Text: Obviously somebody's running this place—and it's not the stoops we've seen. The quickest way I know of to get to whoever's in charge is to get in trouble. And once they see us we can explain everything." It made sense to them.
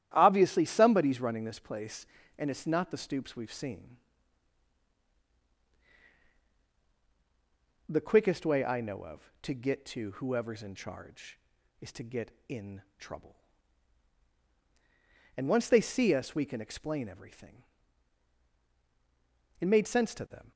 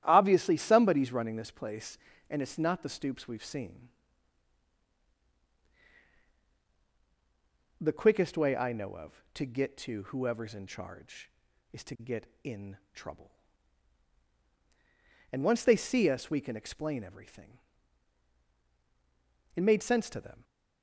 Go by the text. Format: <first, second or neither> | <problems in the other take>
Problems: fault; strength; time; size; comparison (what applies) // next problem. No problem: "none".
neither | starts louder than the rest; strong; the same in both // pauses between "in" and "trouble"; slight; the same in both